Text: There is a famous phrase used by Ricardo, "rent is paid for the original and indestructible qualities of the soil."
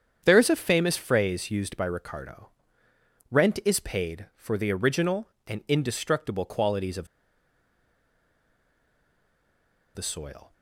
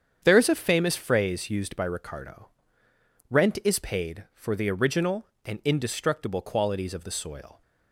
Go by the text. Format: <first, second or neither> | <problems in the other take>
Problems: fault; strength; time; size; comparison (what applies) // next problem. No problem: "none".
second | starts louder than the rest; strong; until 1.2 s; 8 dB; strong in the second // pauses between "of" and "the"; strong; at 7.0 s; 2.8 s long